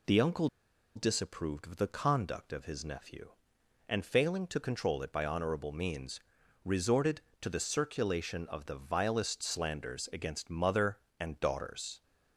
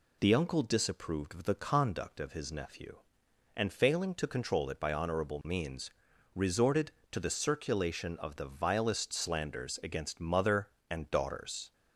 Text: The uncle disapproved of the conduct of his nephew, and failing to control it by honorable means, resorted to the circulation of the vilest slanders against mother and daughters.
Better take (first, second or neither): second